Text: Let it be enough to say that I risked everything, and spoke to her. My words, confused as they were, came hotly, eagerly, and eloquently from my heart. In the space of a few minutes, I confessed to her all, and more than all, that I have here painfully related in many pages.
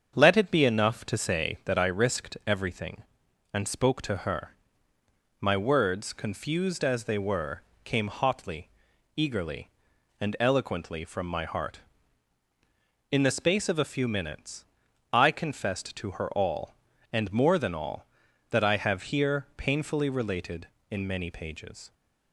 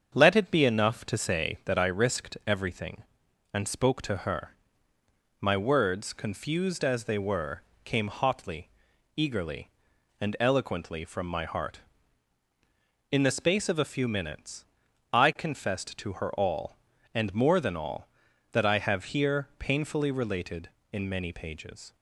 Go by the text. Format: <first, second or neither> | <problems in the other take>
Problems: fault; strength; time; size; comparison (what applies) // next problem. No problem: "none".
neither | starts louder than the rest; strong; the same in both